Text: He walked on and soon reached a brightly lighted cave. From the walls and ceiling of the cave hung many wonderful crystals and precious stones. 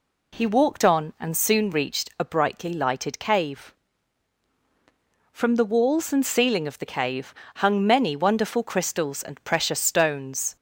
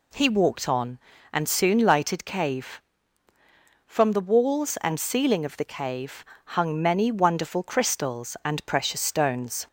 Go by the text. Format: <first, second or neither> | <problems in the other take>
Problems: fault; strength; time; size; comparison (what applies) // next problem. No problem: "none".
first | skips "reached a brightly"; at 1.7 s // pauses between "cave" and "hung"; slight; at 6.2 s; 0.20 s long; slight in the first